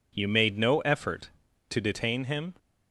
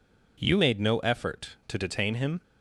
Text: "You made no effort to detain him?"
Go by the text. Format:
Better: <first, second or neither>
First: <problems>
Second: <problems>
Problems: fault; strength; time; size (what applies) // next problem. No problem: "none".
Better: neither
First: none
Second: none